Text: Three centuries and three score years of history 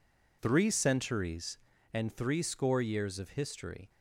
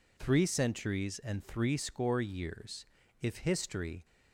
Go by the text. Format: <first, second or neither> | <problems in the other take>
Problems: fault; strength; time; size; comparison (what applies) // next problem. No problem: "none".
first | says "if" for "of"; at 3.2 s